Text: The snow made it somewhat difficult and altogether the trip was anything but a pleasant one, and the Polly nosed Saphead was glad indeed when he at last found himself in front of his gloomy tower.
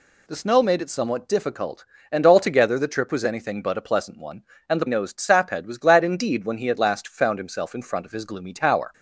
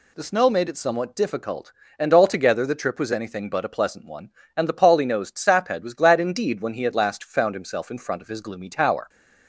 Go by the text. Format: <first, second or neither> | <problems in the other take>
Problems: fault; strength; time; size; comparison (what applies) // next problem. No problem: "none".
second | skips "Polly"; at 4.8 s